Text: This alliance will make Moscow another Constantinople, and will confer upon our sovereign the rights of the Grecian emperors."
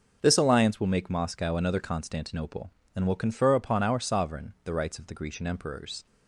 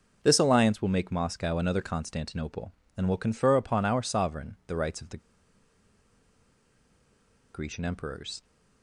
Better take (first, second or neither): first